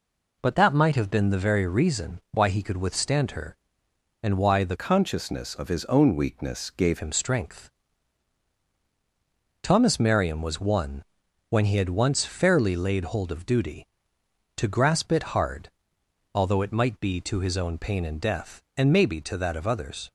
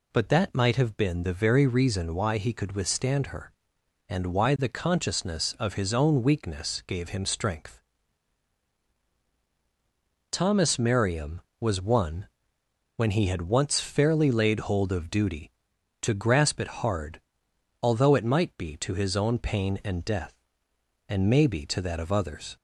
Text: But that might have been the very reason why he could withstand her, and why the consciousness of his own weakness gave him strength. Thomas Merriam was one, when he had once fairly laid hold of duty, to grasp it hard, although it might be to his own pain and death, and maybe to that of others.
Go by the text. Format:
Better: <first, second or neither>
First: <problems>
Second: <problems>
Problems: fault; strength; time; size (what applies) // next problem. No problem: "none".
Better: second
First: changes voice from "consciousness" to "gave"; from 4.7 to 7.0 s; 2.3 s long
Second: none